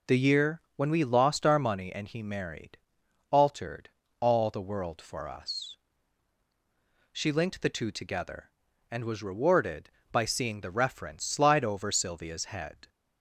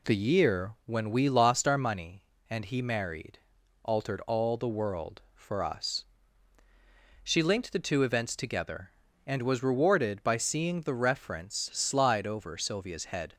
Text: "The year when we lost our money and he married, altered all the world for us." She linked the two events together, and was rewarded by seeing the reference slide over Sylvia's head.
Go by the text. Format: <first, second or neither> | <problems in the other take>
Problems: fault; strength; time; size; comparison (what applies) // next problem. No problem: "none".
second | pauses between "altered" and "all"; slight; at 3.8 s; 0.30 s long // skips "events"; at 7.9 s